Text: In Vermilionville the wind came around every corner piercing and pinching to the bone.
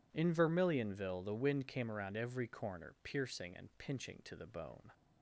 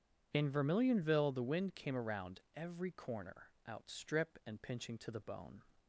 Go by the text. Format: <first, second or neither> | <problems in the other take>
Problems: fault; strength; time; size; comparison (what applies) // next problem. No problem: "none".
first | pauses between "around" and "every"; slight; at 2.3 s; 0.16 s long // says "outstrip" for "piercing"; at 3.6 s